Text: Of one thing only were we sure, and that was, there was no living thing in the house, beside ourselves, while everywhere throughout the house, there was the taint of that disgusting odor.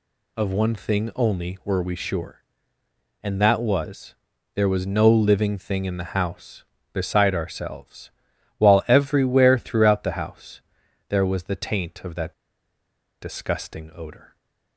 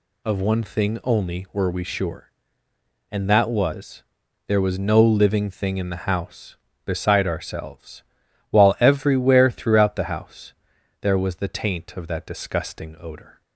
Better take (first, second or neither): second